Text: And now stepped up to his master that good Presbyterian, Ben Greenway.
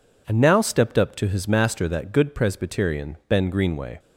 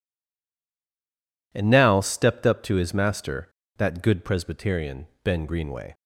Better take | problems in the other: first | stays silent before the first word; noticeable; until 1.5 s; 1.5 s long

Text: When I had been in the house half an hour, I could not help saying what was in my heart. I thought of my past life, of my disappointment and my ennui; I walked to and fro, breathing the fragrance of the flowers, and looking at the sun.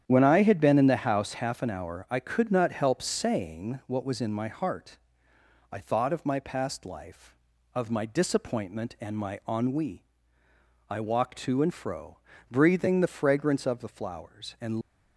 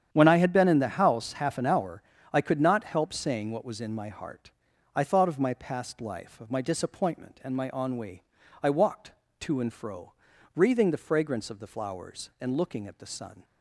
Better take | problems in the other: second | starts louder than the rest; strong; until 1.0 s; 9.5 dB; strong in the second // stops before "looking at the sun"; at 14.8 s

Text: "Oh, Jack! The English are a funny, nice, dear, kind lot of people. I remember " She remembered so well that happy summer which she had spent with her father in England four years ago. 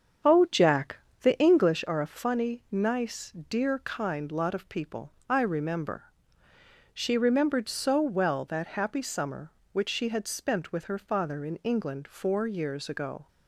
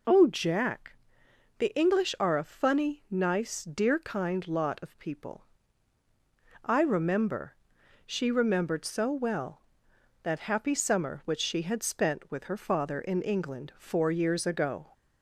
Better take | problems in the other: second | starts louder than the rest; strong; until 1.8 s; 8 dB

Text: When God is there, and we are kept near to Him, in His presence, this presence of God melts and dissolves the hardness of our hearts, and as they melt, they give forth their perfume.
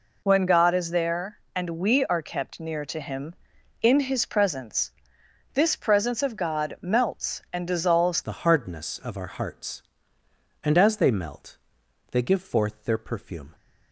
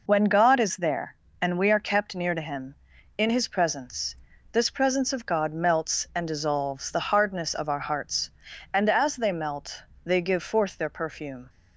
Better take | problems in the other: second | changes voice at "the"; from 8.2 s on; 5.3 s long

